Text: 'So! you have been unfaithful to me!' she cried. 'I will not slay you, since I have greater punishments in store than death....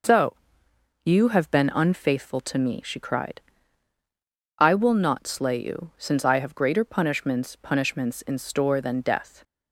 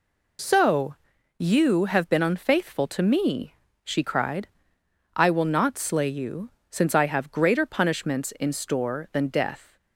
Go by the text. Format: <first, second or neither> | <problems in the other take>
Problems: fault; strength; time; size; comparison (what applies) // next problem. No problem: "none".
second | says "punishments" twice; at 7.5 s